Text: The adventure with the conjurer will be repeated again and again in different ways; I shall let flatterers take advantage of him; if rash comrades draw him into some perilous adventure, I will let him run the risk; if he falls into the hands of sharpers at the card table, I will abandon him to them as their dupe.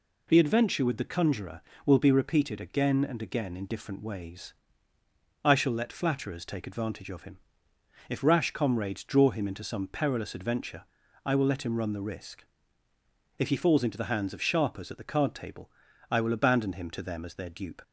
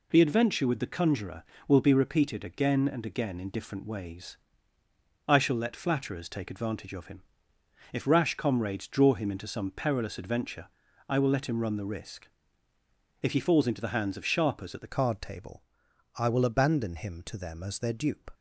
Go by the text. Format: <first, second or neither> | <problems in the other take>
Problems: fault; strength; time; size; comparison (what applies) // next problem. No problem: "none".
first | changes voice at "card"; from 14.8 s on; 3.5 s long